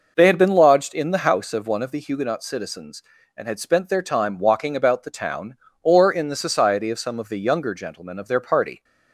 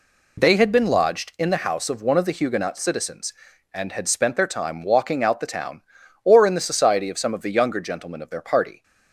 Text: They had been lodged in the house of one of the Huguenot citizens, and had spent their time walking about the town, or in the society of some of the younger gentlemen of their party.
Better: first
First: none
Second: says "out" for "about"; at 5.2 s

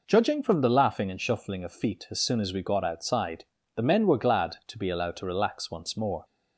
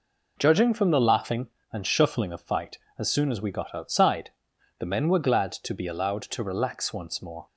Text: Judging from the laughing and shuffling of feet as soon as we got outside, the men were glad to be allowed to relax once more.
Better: first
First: none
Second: says "fight" for "feet"; at 2.4 s

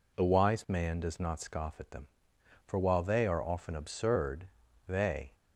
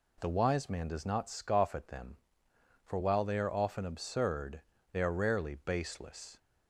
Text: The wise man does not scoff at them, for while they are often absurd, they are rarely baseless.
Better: second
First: stops before "are rarely baseless"; at 5.3 s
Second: none

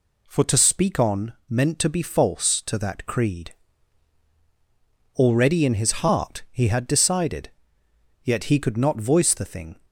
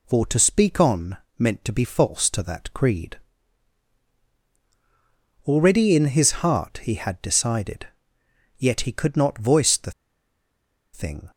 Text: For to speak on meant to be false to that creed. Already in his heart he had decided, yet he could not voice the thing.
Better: first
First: pauses between "on" and "meant"; slight; at 1.3 s; 0.16 s long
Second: pauses between "on" and "meant"; slight; at 1.1 s; 0.20 s long // pauses between "the" and "thing"; at 9.8 s; 1.0 s long

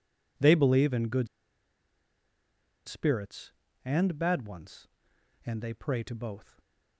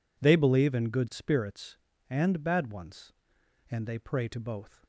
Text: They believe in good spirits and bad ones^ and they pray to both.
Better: second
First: pauses between "good" and "spirits"; strong; at 1.2 s; 1.6 s long // stays silent after the last word; slight; from 6.4 s on; 0.5 s long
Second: none

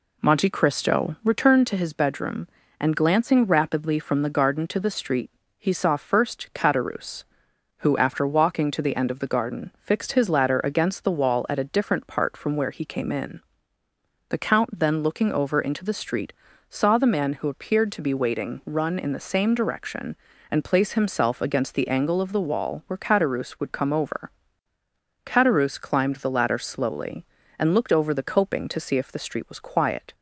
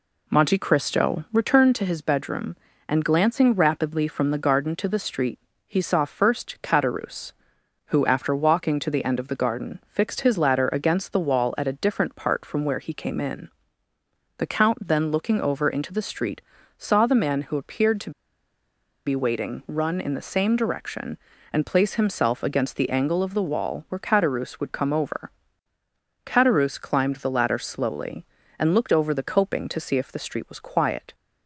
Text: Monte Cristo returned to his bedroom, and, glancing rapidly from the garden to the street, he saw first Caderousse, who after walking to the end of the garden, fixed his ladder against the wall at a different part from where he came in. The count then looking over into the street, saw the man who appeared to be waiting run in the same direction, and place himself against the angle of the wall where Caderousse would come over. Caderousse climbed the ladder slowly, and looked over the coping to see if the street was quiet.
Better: first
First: none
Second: pauses between "to" and "be"; noticeable; at 18.1 s; 0.95 s long

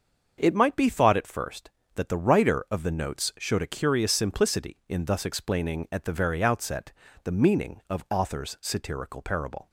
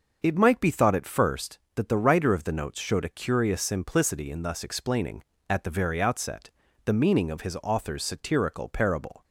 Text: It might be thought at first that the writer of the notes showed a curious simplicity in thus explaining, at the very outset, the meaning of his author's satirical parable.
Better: second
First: starts louder than the rest; until 1.3 s; 6.5 dB // skips "his"; at 8.0 s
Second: starts louder than the rest; until 1.2 s; 6.5 dB

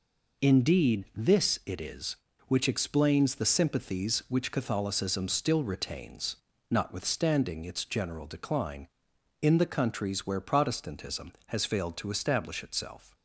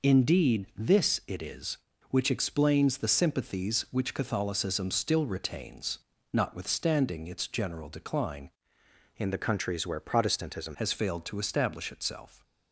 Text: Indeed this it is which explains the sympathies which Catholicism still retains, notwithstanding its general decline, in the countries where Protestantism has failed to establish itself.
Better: first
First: none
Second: changes voice from "in" to "Protestantism"; from 9.1 to 10.7 s; 1.6 s long

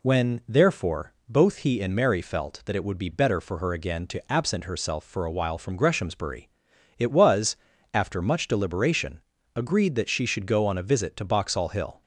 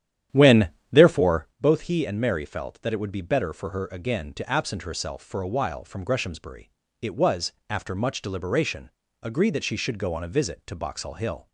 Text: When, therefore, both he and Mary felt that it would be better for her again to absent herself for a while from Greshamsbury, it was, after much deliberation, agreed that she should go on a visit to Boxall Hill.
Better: first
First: none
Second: starts louder than the rest; strong; until 1.6 s; 10.5 dB

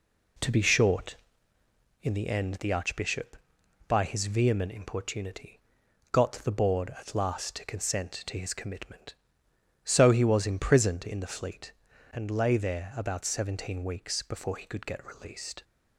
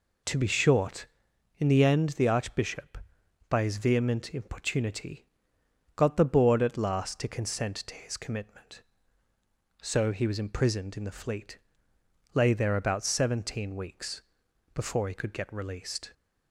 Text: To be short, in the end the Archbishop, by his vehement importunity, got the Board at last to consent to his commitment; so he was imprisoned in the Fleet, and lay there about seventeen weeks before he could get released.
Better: first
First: none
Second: skips "and"; at 11.9 s // pauses between "weeks" and "before"; noticeable; at 14.2 s; 0.52 s long

